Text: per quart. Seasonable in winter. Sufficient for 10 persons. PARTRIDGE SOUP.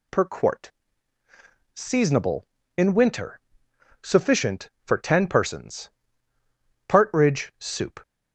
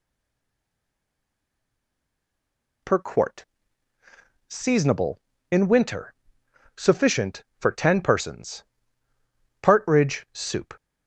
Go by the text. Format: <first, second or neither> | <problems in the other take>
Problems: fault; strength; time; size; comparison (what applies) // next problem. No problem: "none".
first | stays silent before the first word; strong; until 2.8 s; 2.8 s long